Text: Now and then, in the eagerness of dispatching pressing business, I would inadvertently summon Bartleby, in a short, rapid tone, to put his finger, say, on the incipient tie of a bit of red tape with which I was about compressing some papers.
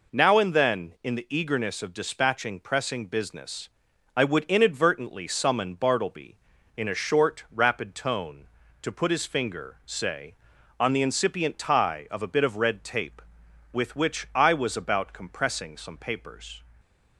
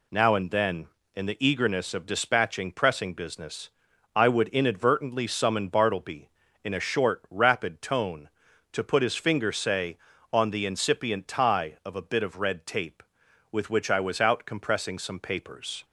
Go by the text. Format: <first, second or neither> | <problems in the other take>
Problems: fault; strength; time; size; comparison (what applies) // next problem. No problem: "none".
first | says "out" for "about"; at 14.1 s